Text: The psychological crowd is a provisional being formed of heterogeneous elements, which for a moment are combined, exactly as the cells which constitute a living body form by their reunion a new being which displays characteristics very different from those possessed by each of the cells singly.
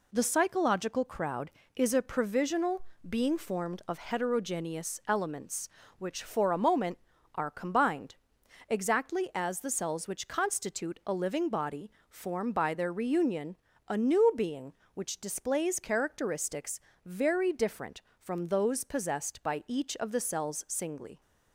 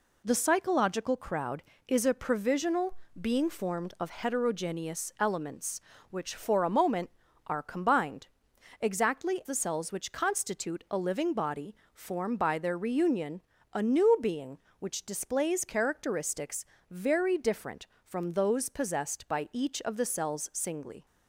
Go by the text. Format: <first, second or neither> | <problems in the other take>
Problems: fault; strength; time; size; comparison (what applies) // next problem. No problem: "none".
first | pauses between "provisional" and "being"; slight; at 2.9 s; 0.22 s long; slight in the first // skips "as"; at 9.4 s // pauses between "body" and "form"; slight; at 11.7 s; 0.18 s long; slight in the first // pauses between "reunion" and "a"; slight; at 13.4 s; 0.32 s long; slight in the first // pauses between "characteristics" and "very"; slight; at 16.6 s; 0.24 s long; slight in the first